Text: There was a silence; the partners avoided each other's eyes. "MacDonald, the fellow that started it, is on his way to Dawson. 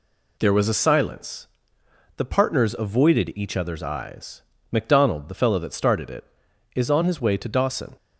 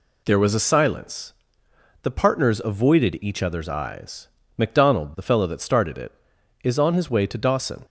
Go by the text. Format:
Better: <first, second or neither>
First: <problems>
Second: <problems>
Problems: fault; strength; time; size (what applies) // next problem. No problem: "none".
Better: neither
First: none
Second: none